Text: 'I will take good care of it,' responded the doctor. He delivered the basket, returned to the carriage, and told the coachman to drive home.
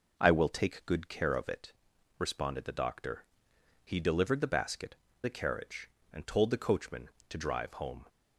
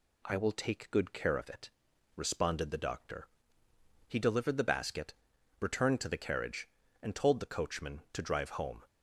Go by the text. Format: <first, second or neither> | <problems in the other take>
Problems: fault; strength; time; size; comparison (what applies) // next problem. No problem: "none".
second | skips "returned to"; at 5.0 s